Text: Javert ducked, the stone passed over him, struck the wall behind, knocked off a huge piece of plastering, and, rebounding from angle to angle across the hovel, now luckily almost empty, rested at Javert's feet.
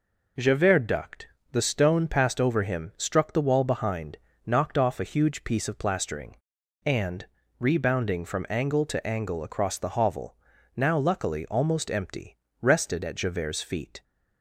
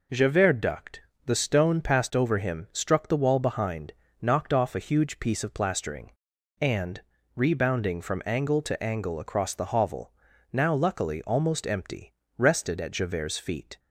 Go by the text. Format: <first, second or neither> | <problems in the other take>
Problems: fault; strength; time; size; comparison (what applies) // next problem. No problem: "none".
neither | none